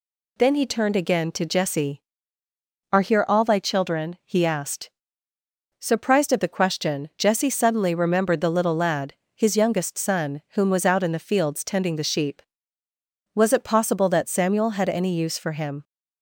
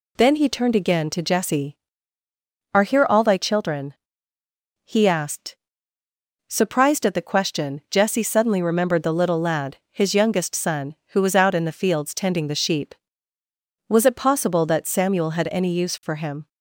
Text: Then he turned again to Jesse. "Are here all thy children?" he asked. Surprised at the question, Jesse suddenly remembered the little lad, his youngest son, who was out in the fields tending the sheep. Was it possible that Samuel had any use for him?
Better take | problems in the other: second | says "whom" for "who"; at 10.5 s

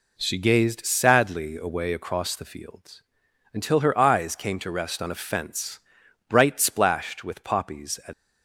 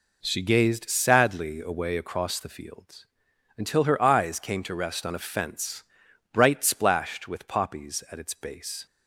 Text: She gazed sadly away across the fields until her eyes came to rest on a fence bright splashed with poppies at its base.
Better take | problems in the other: second | pauses between "fields" and "until"; noticeable; at 3.0 s; 0.52 s long; noticeable in the second // pauses between "fence" and "bright"; noticeable; at 5.7 s; 0.48 s long; noticeable in the second // stops before "its base"; at 8.1 s

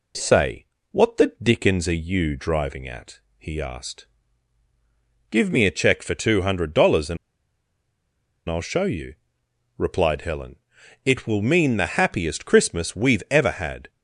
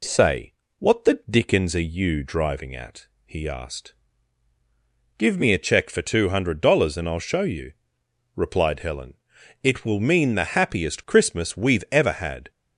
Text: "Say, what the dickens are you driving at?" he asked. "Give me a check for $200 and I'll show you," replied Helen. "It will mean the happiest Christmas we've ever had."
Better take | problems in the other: second | pauses between "and" and "I'll"; strong; at 7.1 s; 1.3 s long

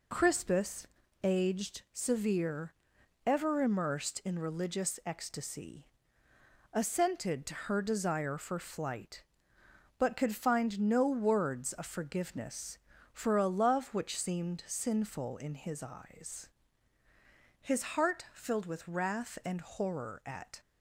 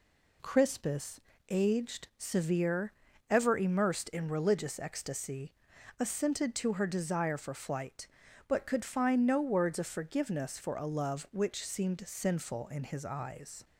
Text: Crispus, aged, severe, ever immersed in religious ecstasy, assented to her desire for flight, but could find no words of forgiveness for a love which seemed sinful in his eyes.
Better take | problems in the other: second | goes on to say "His heart filled with wrath and horror at"; strong; from 17.5 s on; 3.0 s long

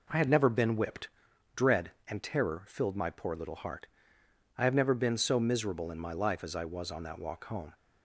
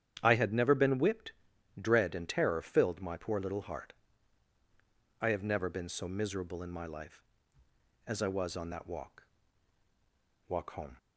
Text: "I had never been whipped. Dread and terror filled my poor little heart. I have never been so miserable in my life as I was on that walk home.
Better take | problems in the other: first | starts louder than the rest; strong; until 1.2 s; 9.5 dB // says "walk" twice; at 10.4 s

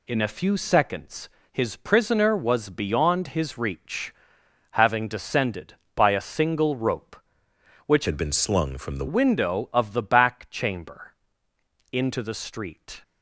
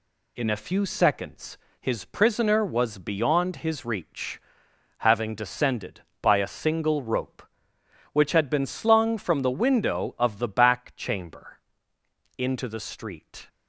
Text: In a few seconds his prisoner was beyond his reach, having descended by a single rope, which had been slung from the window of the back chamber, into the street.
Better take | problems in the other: second | pauses between "seconds" and "his"; slight; at 1.2 s; 0.24 s long; slight in the second // changes voice from "had" to "the"; from 8.0 to 9.0 s; 1.0 s long

